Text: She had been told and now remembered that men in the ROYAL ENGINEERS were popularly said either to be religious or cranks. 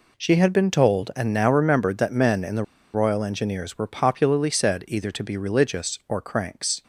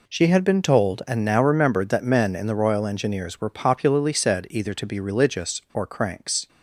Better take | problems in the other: second | pauses between "the" and "ROYAL"; slight; at 2.6 s; 0.29 s long

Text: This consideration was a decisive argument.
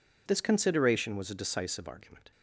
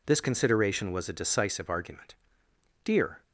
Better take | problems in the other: first | goes on to say "Dear"; slight; from 2.8 s on; 0.40 s long

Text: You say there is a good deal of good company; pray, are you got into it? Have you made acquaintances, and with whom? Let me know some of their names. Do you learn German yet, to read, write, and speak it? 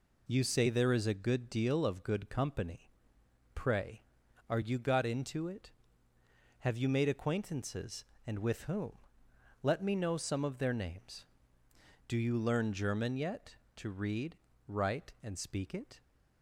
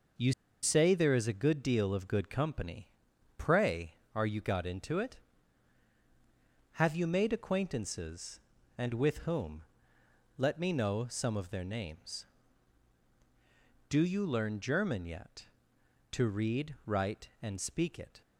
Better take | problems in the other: first | pauses between "You" and "say"; slight; at 0.3 s; 0.30 s long

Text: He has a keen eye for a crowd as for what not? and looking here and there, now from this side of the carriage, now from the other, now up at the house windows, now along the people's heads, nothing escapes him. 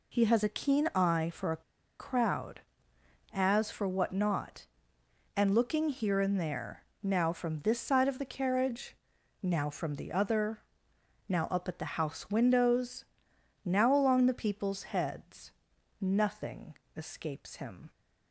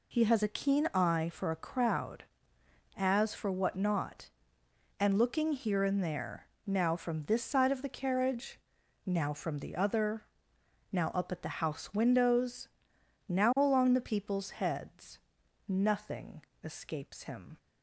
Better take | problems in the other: second | pauses between "a" and "crowd"; at 1.6 s; 0.36 s long // pauses between "nothing" and "escapes"; slight; at 16.7 s; 0.24 s long; slight in the second

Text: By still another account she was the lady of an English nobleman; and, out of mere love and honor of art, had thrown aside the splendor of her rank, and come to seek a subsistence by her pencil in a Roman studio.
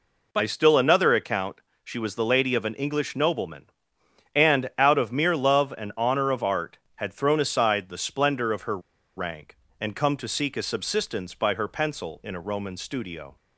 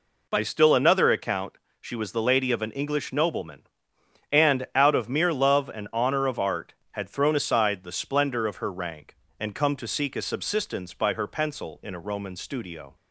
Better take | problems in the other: second | pauses between "account" and "she"; slight; at 1.5 s; 0.26 s long; slight in the second // pauses between "her" and "rank"; at 8.7 s; 0.38 s long

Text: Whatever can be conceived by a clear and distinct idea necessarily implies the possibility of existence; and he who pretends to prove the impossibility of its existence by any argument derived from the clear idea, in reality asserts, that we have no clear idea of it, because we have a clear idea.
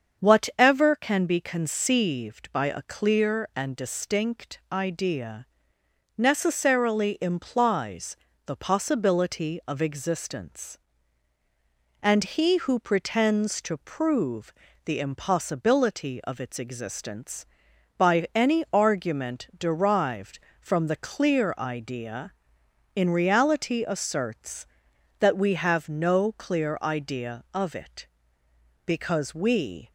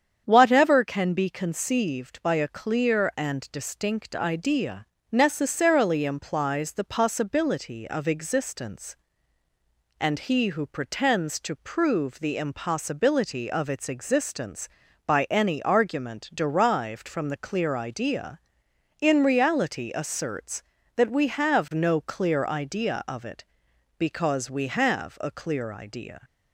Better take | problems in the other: second | starts louder than the rest; until 1.2 s; 7 dB; strong in the second // pauses between "idea" and "necessarily"; noticeable; at 5.4 s; 0.72 s long; slight in the second // pauses between "implies" and "the"; slight; at 8.1 s; 0.28 s long // pauses between "prove" and "the"; slight; at 14.5 s; 0.30 s long // stops before "have a clear idea"; at 29.8 s

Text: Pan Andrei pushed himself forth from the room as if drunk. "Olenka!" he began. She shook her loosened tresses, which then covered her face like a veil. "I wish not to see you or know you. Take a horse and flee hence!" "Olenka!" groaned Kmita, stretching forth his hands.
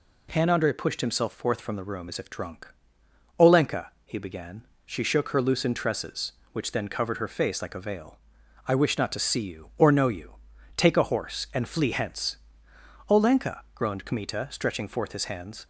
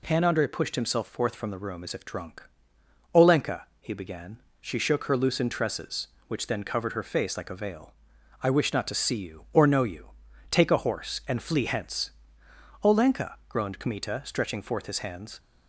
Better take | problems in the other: neither | none

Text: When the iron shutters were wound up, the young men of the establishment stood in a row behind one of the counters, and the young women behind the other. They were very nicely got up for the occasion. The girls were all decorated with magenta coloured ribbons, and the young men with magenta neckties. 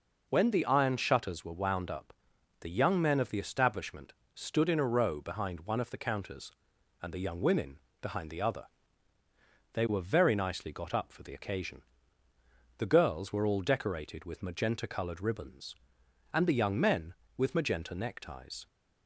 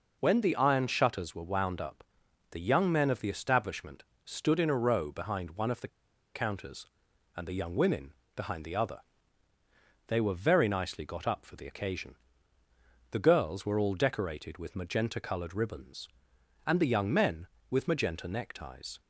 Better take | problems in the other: first | pauses between "establishment" and "stood"; slight; at 4.0 s; 0.24 s long; slight in the first // pauses between "the" and "counters"; noticeable; at 5.8 s; 0.46 s long // pauses between "women" and "behind"; slight; at 8.1 s; 0.22 s long; slight in the first

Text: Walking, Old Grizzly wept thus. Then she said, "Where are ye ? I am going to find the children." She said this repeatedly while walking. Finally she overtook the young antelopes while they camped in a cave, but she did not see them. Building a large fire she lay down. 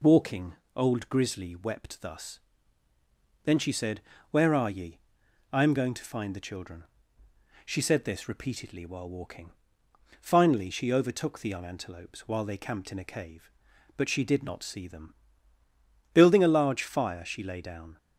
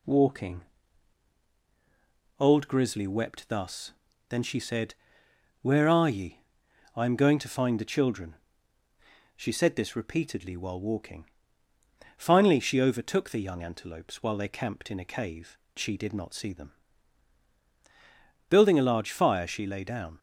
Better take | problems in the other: first | skips "but"; at 15.6 s

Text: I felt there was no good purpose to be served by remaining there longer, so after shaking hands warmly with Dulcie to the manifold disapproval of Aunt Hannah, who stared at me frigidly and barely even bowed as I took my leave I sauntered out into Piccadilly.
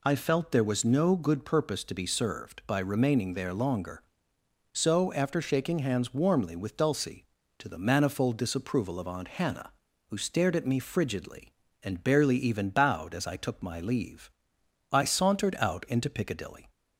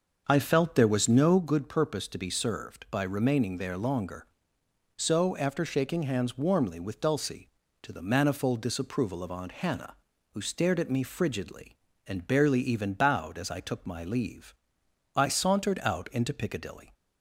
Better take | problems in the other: first | starts louder than the rest; until 1.5 s; 6.5 dB // pauses between "leave" and "I"; noticeable; at 14.5 s; 0.60 s long; noticeable in the first

